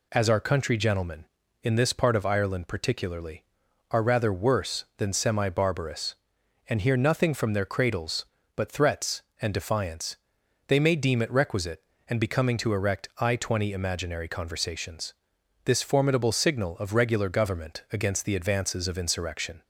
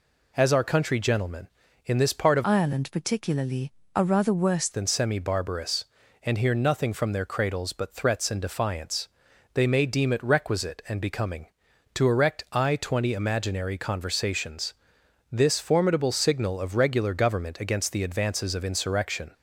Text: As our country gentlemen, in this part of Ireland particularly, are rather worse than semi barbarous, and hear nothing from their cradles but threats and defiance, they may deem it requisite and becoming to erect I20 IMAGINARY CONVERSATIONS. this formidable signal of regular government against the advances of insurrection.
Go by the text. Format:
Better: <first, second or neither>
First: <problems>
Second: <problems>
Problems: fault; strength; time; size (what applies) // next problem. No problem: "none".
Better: first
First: none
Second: changes voice from "Ireland" to "worse"; from 2.4 to 4.6 s; 2.2 s long